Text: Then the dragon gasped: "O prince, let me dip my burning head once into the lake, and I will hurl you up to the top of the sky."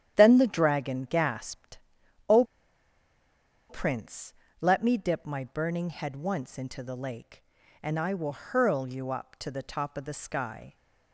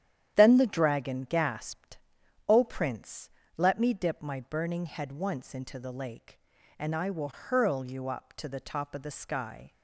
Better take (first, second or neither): second